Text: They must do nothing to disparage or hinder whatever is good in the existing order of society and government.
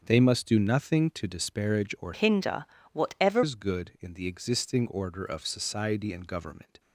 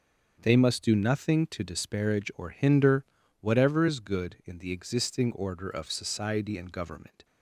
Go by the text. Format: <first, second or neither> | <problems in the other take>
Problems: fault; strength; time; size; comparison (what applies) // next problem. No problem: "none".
second | starts louder than the rest; until 1.0 s; 7 dB; strong in the second // changes voice from "hinder" to "whatever"; from 2.1 to 3.4 s; 1.3 s long // pauses between "hinder" and "whatever"; slight; at 2.6 s; 0.28 s long; also in the second